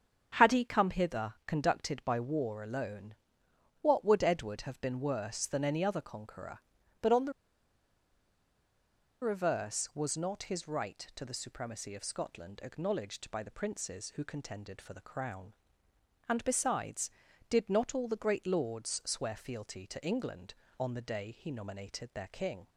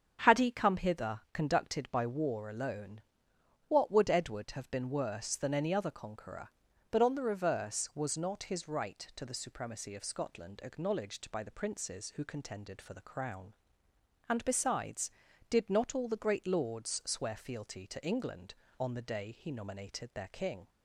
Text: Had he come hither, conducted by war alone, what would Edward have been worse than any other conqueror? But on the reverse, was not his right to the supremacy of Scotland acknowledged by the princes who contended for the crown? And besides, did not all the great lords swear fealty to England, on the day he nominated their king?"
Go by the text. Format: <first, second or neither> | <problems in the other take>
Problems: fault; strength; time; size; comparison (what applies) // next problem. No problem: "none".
second | starts louder than the rest; strong; until 1.4 s; 7.5 dB; strong in the second // pauses between "the" and "reverse"; strong; at 7.3 s; 1.9 s long